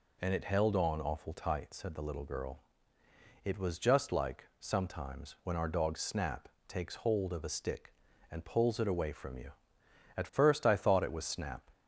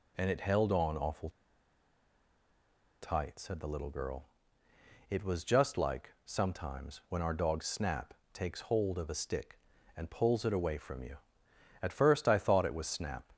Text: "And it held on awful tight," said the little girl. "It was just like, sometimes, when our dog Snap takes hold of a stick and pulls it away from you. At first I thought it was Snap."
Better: first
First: pauses between "Snap" and "takes"; slight; at 6.4 s; 0.18 s long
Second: pauses between "awful" and "tight"; strong; at 1.2 s; 1.7 s long // pauses between "Snap" and "takes"; slight; at 8.1 s; 0.18 s long

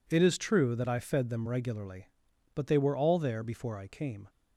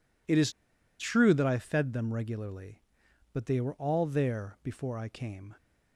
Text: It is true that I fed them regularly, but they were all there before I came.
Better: first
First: none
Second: pauses between "is" and "true"; noticeable; at 0.5 s; 0.48 s long

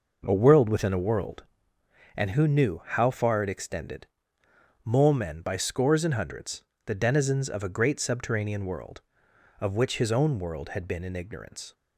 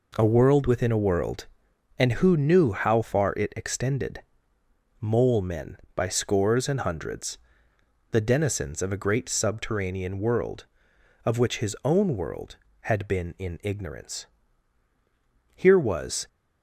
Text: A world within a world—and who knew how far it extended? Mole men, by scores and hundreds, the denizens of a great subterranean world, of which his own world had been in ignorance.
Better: first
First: none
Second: goes on to say "Here was"; noticeable; from 15.5 s on; 0.72 s long

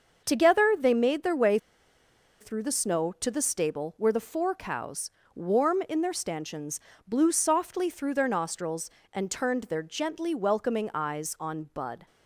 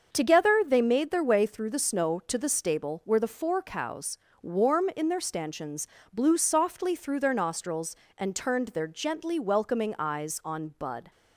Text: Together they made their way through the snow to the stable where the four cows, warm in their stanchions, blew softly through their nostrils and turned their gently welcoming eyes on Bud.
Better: second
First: starts louder than the rest; until 1.2 s; 6.5 dB // pauses between "way" and "through"; noticeable; at 1.5 s; 0.83 s long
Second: starts louder than the rest; until 1.1 s; 6.5 dB

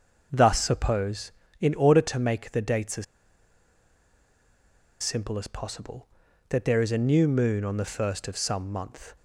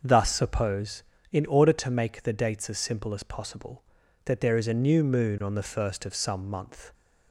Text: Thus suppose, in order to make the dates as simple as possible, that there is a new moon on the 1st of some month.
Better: second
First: starts louder than the rest; until 1.3 s; 6.5 dB // pauses between "as" and "simple"; strong; at 3.0 s; 1.9 s long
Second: starts louder than the rest; until 1.0 s; 6.5 dB

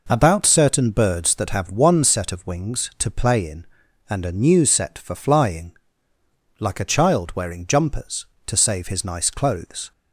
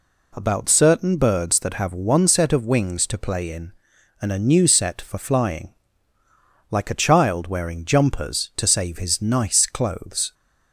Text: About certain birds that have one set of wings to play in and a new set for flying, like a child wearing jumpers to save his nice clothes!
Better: neither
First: none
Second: none

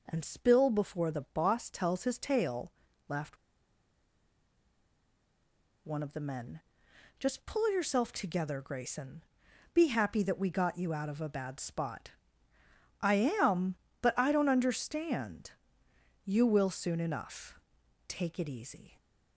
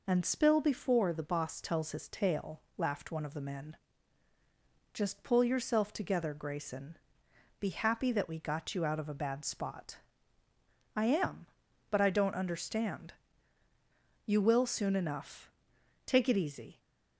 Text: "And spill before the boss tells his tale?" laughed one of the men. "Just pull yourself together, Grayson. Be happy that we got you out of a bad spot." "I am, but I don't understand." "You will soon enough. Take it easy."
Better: second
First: pauses between "laughed" and "one"; strong; at 3.3 s; 2.4 s long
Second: none

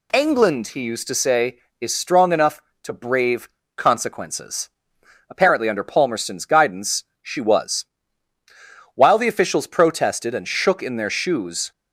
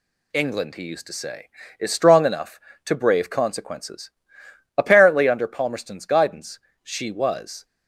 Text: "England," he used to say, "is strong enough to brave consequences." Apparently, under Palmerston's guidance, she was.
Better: second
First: pauses between "brave" and "consequences"; slight; at 3.4 s; 0.30 s long // goes on to say "While the officials protested and shook in their shoes"; strong; from 8.9 s on; 2.7 s long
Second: none

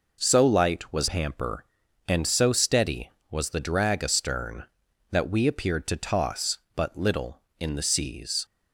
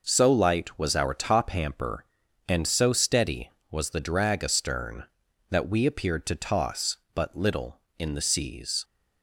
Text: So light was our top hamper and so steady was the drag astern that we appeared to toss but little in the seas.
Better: second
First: skips "our top"; at 1.0 s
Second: none

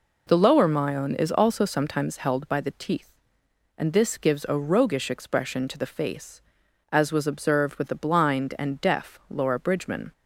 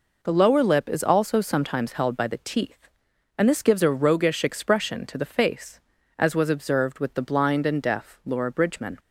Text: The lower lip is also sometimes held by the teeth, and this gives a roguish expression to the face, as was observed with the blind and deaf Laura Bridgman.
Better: second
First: says "mion" for "lip"; at 0.6 s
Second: none

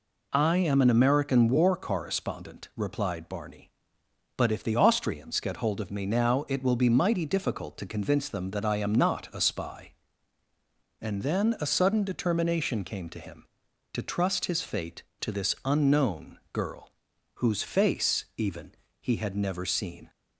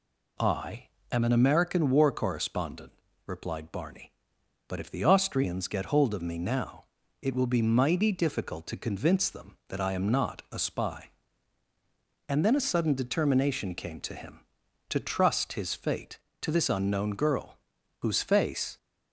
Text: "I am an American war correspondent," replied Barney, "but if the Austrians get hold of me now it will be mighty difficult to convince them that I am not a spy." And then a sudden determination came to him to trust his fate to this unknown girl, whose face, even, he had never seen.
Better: first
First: none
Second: pauses between "I" and "am"; slight; at 0.8 s; 0.22 s long // pauses between "now" and "it"; at 6.8 s; 0.38 s long // stops before "even he had never seen"; at 18.7 s

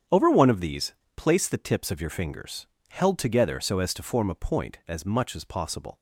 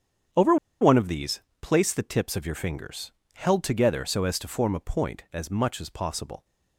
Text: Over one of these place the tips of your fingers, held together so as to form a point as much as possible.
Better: first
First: starts louder than the rest; strong; until 1.3 s; 8.5 dB // pauses between "these" and "place"; slight; at 0.9 s; 0.24 s long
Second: starts louder than the rest; strong; until 1.8 s; 8.5 dB // pauses between "Over" and "one"; slight; at 0.5 s; 0.25 s long // pauses between "these" and "place"; slight; at 1.4 s; 0.22 s long

